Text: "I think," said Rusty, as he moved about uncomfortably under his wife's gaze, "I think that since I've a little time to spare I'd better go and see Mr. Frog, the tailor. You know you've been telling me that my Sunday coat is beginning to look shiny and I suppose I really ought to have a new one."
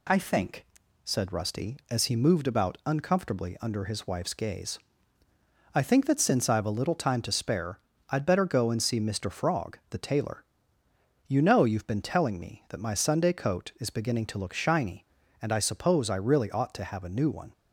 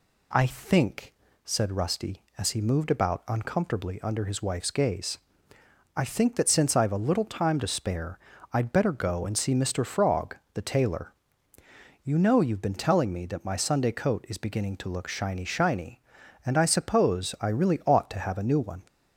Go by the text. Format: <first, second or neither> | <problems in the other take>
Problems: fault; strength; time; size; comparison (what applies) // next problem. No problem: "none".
first | pauses between "spare" and "I'd"; slight; at 8.1 s; 0.36 s long; slight in the first // says "shiny" twice; at 15.4 s